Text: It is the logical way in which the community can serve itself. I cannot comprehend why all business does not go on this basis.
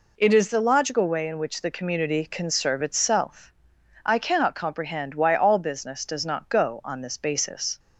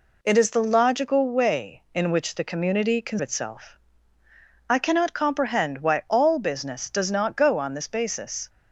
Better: first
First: none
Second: skips "serve"; at 3.1 s

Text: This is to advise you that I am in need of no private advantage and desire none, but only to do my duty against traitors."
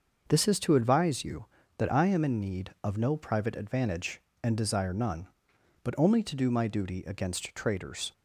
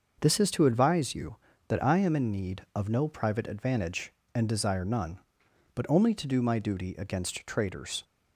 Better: neither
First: starts louder than the rest; until 1.3 s; 6 dB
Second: starts louder than the rest; until 1.2 s; 6 dB

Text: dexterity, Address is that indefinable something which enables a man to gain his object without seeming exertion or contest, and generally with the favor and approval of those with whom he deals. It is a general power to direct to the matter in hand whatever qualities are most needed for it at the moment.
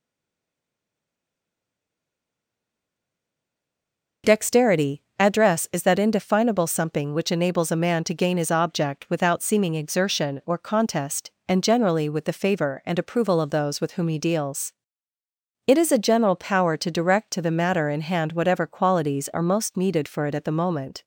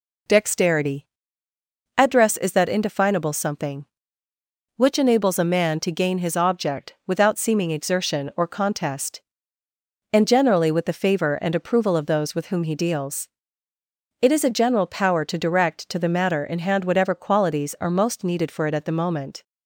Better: second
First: stays silent before the first word; strong; until 4.2 s; 4.2 s long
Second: none

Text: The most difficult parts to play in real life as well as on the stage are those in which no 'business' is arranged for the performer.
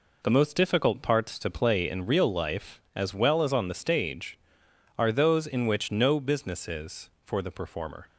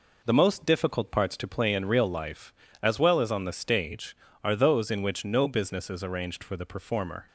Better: second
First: skips "arranged"; at 7.1 s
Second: none

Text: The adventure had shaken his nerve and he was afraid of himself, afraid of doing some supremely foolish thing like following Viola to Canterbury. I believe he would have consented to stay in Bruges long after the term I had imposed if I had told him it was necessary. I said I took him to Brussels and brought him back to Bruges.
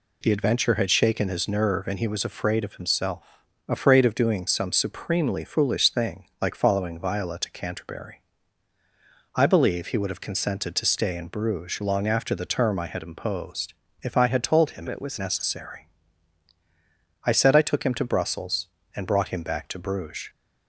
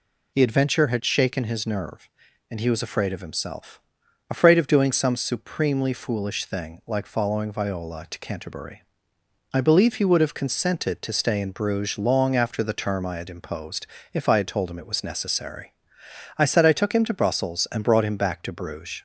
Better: second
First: pauses between "imposed" and "if"; slight; at 13.7 s; 0.30 s long // changes voice from "it" to "was"; from 14.8 to 15.1 s; 0.3 s long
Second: pauses between "imposed" and "if"; slight; at 13.8 s; 0.26 s long

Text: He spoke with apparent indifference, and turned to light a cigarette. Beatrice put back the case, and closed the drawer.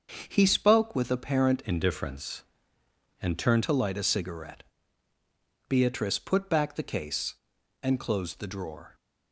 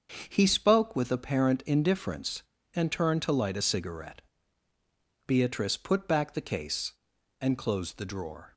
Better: second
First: starts louder than the rest; until 1.2 s; 7 dB // changes voice from "indifference" to "turned"; from 1.6 to 3.6 s; 2.0 s long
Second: starts louder than the rest; until 1.2 s; 6.5 dB

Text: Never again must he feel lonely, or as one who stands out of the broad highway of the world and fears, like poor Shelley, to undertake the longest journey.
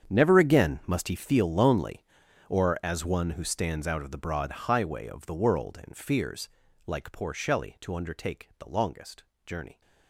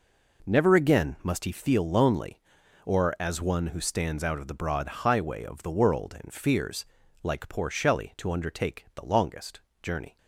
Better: second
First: gets quieter; strong; throughout; 16.5 dB // pauses between "longest" and "journey"; slight; at 9.2 s; 0.22 s long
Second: pauses between "longest" and "journey"; slight; at 9.6 s; 0.22 s long

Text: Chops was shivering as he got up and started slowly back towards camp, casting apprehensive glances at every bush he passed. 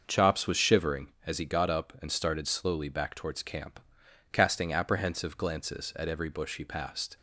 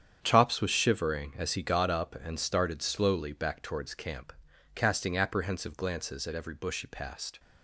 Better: first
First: starts louder than the rest; noticeable; until 1.0 s; 6 dB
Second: gets quieter; strong; throughout; 11 dB // starts louder than the rest; strong; until 1.2 s; 8.5 dB

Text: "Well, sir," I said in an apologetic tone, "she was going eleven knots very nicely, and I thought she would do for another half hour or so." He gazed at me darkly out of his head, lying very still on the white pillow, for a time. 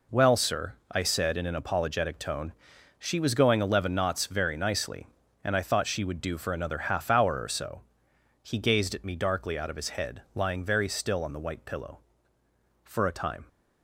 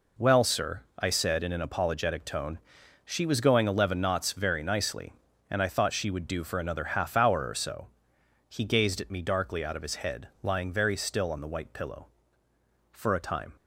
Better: neither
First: none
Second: none

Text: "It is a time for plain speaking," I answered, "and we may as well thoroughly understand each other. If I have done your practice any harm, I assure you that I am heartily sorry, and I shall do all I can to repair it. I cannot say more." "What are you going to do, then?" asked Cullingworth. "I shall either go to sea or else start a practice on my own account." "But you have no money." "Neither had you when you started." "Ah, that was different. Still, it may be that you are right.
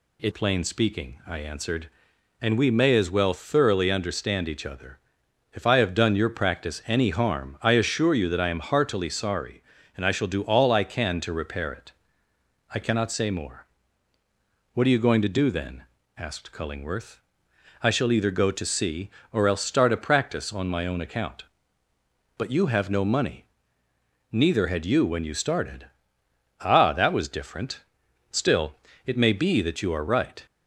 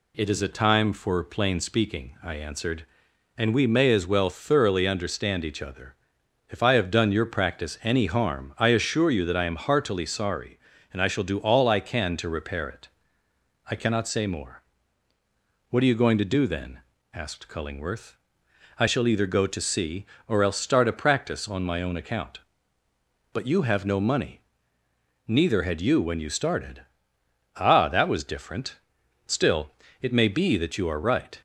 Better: second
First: skips "is a time for"; at 0.3 s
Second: none

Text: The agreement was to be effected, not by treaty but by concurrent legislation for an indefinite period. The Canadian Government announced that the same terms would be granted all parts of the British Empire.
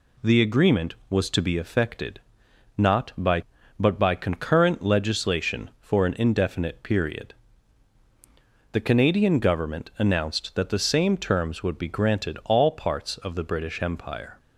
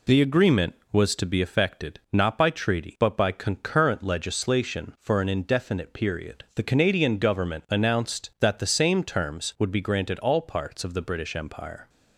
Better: second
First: skips "treaty"; at 3.5 s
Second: none

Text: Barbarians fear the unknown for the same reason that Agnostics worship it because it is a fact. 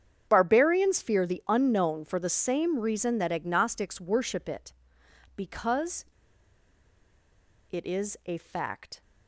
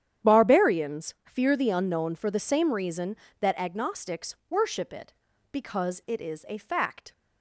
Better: second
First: starts louder than the rest; strong; until 1.2 s; 8.5 dB // pauses between "because" and "it"; strong; at 6.0 s; 1.6 s long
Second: starts louder than the rest; strong; until 1.3 s; 9.5 dB

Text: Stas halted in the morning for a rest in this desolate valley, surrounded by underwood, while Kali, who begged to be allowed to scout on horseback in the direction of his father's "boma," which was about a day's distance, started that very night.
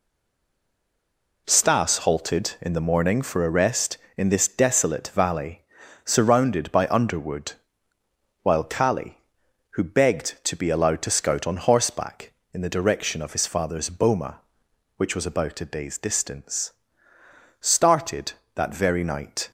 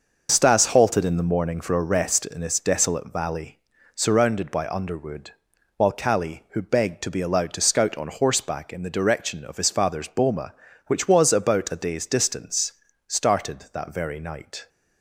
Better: second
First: stays silent before the first word; noticeable; until 1.4 s; 1.4 s long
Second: none

